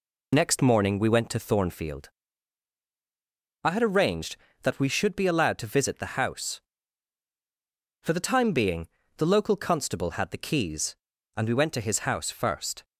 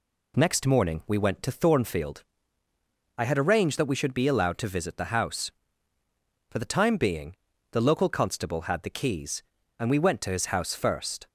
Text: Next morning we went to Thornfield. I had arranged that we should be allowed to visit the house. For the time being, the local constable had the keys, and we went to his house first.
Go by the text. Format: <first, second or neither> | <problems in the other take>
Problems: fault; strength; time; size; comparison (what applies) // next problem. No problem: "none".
second | loses the start of "Next"; at 0.3 s; 55 ms